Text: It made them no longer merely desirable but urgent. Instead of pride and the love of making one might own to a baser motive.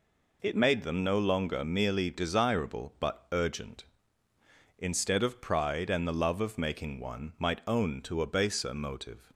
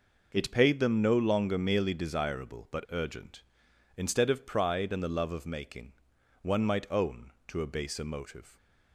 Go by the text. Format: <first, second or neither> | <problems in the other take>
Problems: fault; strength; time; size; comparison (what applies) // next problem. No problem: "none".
first | says "paid" for "made"; at 0.5 s // pauses between "making" and "one"; noticeable; at 5.9 s; 0.50 s long